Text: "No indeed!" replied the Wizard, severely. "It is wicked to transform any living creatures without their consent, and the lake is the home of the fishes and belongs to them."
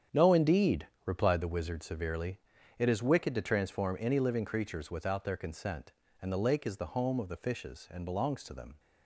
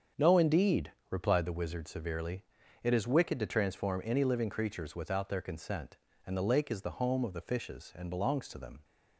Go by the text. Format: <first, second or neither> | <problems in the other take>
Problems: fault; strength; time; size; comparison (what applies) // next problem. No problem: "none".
second | gets quieter; strong; throughout; 11.5 dB // starts louder than the rest; strong; until 1.3 s; 8.5 dB; strong in the second